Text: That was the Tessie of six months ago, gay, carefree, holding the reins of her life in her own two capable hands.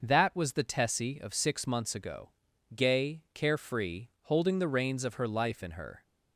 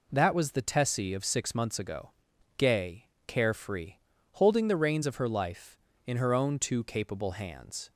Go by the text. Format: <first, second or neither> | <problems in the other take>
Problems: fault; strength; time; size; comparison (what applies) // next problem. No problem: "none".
second | starts louder than the rest; noticeable; until 1.0 s; 6 dB // stops before "own two capable hands"; at 6.0 s